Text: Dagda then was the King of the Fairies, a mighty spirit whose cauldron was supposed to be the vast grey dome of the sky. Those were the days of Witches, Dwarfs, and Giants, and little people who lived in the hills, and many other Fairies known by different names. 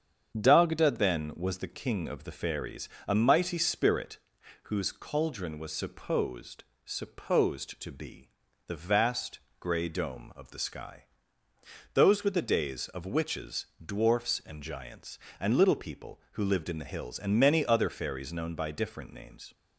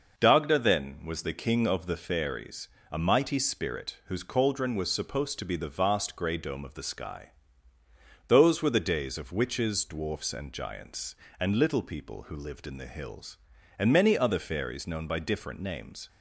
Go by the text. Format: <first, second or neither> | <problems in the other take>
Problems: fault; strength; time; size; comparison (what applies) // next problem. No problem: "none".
second | starts louder than the rest; strong; until 1.4 s; 7.5 dB // pauses between "spirit" and "whose"; noticeable; at 4.1 s; 0.46 s long // says "supposed" twice; at 6.8 s // pauses between "be" and "the"; slight; at 8.2 s; 0.36 s long // pauses between "vast" and "grey"; slight; at 9.3 s; 0.20 s long